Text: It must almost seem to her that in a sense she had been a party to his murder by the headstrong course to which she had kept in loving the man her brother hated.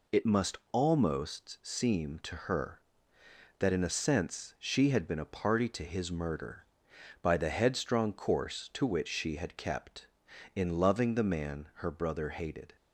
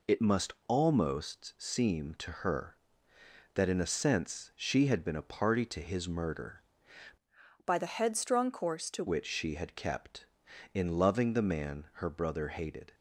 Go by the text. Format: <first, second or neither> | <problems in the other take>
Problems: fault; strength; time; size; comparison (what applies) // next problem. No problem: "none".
first | pauses between "must" and "almost"; slight; at 0.5 s; 0.16 s long; slight in the first // changes voice from "by" to "to"; from 7.6 to 9.0 s; 1.4 s long